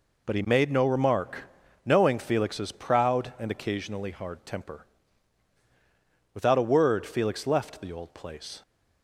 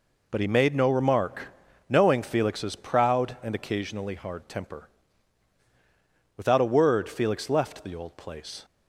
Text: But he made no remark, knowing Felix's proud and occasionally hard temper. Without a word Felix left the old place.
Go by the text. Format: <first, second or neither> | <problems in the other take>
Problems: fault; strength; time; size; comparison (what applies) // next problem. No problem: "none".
neither | none